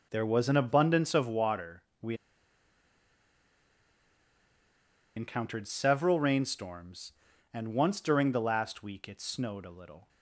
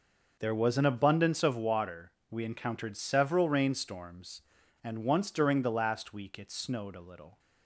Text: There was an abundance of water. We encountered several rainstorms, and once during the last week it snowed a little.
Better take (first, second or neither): second